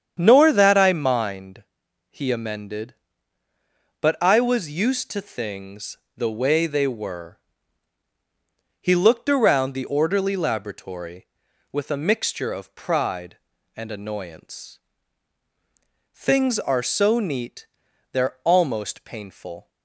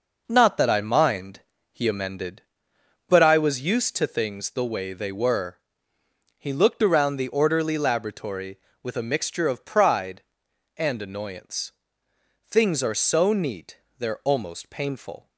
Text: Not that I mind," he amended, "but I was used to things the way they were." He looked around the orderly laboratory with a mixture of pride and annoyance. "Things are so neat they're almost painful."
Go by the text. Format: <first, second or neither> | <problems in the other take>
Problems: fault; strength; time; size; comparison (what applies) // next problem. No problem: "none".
second | starts louder than the rest; strong; until 1.2 s; 8.5 dB // says "Nor" for "Not"; at 0.2 s // pauses between "things" and "the"; slight; at 5.9 s; 0.20 s long // pauses between "neat" and "they're"; at 17.6 s; 0.42 s long; slight in the second